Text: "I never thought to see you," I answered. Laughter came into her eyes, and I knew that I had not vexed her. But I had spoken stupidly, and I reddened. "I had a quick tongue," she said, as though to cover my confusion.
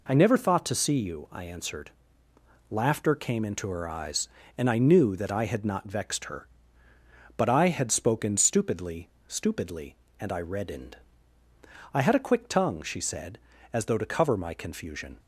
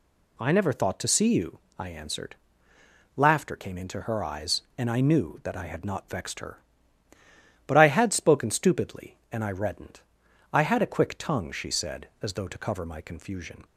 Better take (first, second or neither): second